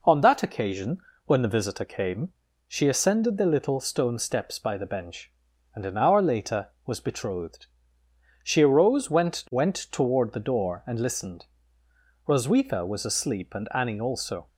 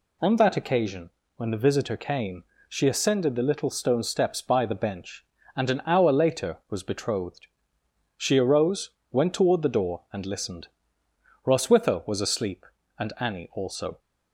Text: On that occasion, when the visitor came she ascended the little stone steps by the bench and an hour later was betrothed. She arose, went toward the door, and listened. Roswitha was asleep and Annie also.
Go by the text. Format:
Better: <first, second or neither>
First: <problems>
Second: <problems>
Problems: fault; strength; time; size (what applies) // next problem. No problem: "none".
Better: second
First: pauses between "came" and "she"; slight; at 2.3 s; 0.36 s long // says "went" twice; at 9.5 s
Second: pauses between "came" and "she"; slight; at 2.4 s; 0.28 s long